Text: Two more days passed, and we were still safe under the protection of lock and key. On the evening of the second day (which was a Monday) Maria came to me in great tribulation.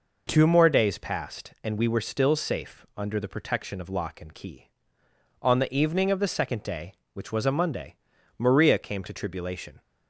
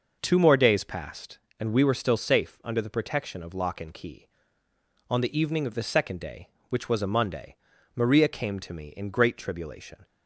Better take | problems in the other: second | skips "me in great"; at 9.1 s

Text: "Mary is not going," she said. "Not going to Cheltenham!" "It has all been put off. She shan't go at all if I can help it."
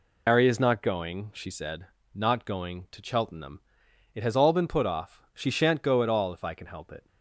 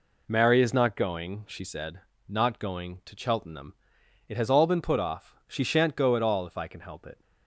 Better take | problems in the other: second | loses the start of "Mary"; at 0.2 s; 135 ms

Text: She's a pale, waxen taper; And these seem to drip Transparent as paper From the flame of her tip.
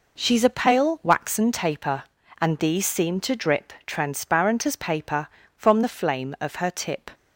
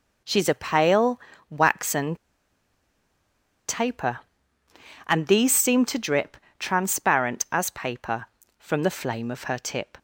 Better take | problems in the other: first | pauses between "waxen" and "taper"; strong; at 2.1 s; 1.5 s long // pauses between "drip" and "Transparent"; slight; at 6.3 s; 0.24 s long

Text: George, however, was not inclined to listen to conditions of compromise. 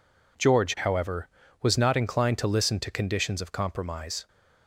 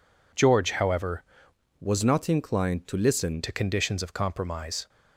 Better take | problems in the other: first | changes voice from "was" to "listen"; from 1.7 to 3.4 s; 1.7 s long

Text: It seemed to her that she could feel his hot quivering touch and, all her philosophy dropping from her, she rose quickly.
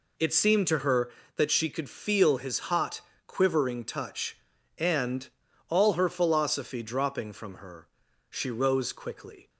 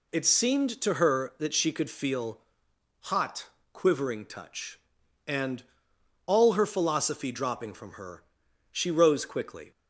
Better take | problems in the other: first | skips "his"; at 2.6 s // pauses between "hot" and "quivering"; slight; at 3.4 s; 0.24 s long; slight in the first

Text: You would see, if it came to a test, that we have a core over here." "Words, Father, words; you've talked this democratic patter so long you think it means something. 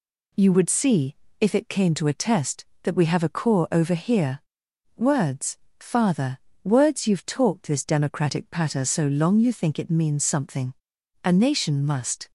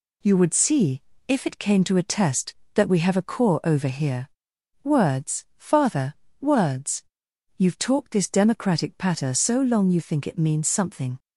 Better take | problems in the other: second | goes on to say "A nation must"; noticeable; from 11.2 s on; 1.0 s long

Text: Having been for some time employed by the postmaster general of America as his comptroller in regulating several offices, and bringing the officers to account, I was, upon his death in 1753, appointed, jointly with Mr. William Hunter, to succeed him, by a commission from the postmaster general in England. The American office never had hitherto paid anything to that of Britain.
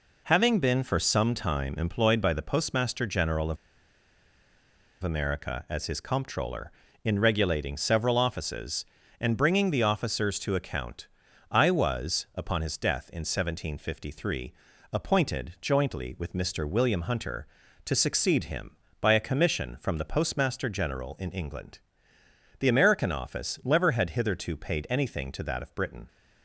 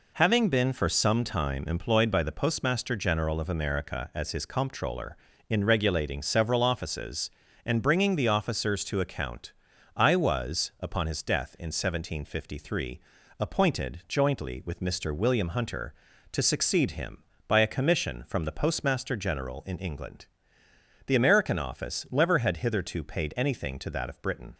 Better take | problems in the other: second | pauses between "of" and "America"; strong; at 3.5 s; 1.4 s long

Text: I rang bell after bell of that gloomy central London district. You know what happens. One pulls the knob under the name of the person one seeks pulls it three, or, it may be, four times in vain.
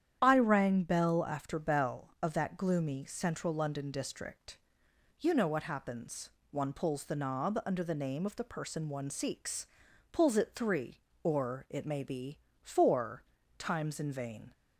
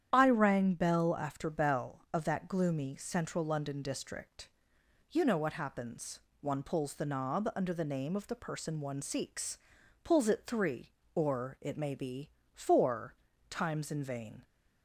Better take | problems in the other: neither | starts louder than the rest; strong; the same in both // pauses between "seeks" and "pulls"; noticeable; the same in both // pauses between "four" and "times"; slight; the same in both

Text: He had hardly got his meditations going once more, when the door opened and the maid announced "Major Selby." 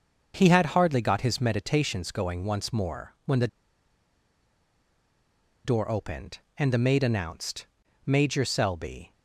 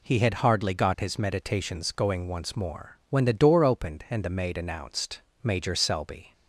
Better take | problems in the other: second | starts louder than the rest; until 1.3 s; 6.5 dB // pauses between "the" and "door"; strong; at 3.4 s; 2.1 s long // pauses between "announced" and "Major"; at 7.6 s; 0.40 s long; slight in the second

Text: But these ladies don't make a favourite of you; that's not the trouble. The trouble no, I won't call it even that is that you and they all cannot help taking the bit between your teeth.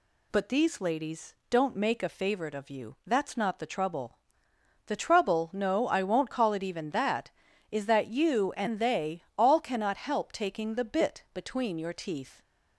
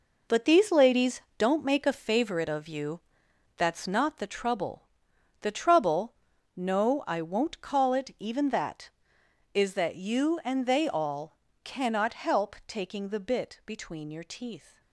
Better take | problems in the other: first | gets quieter; strong; throughout; 10 dB // pauses between "ladies" and "don't"; slight; at 1.2 s; 0.18 s long; slight in the first // pauses between "trouble" and "no"; at 6.1 s; 0.42 s long // pauses between "all" and "cannot"; slight; at 11.3 s; 0.26 s long

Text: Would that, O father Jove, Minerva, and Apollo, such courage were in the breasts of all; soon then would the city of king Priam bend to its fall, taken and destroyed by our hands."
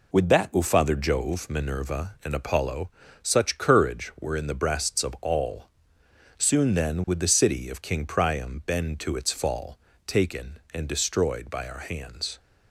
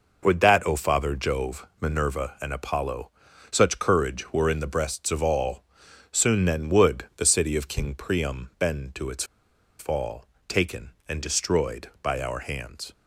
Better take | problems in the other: first | pauses between "its" and "fall"; noticeable; at 9.2 s; 0.55 s long

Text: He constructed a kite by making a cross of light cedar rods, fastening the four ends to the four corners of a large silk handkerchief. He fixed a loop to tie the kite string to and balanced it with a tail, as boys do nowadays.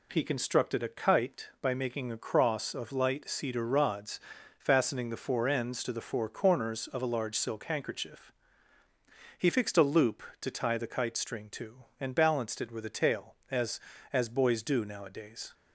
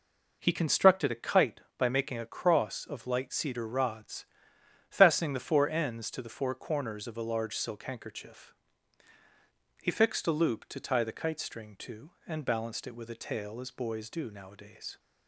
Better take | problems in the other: second | says "as" twice; at 14.1 s

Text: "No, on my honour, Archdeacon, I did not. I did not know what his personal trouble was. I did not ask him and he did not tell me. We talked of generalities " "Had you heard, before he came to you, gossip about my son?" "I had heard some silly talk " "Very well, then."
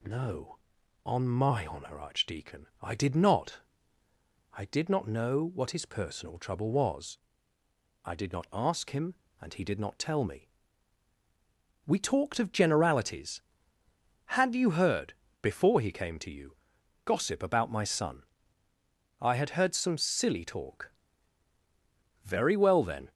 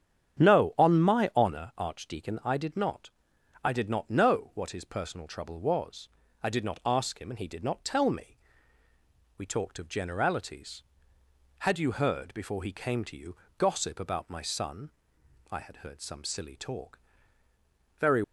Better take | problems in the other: first | starts louder than the rest; strong; until 1.4 s; 8.5 dB // stops before "well then"; at 18.2 s

